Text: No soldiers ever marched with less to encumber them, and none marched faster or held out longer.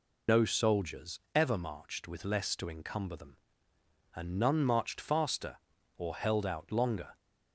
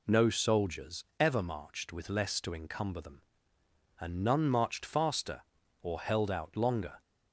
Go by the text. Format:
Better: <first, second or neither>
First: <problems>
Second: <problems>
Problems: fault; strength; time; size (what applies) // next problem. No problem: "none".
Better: second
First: loses the start of "No"; at 0.2 s; 75 ms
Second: none